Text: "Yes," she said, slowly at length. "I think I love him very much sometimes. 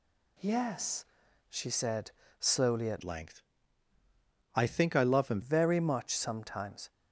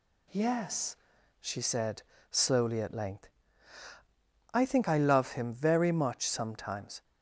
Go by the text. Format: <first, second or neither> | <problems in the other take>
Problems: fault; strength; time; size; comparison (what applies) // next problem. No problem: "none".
second | changes voice from "length" to "him"; from 3.0 to 5.4 s; 2.4 s long